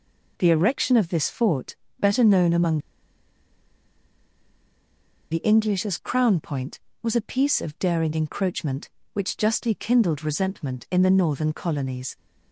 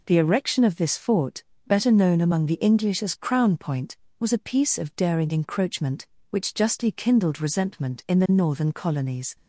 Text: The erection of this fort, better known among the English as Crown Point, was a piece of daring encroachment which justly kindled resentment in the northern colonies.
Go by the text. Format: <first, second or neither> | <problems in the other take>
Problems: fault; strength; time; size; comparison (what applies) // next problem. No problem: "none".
second | pauses between "among" and "the"; strong; at 2.7 s; 2.5 s long